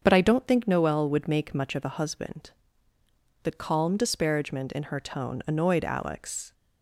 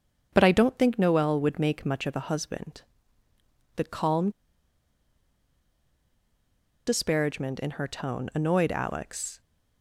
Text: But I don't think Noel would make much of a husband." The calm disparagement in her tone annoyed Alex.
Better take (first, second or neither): first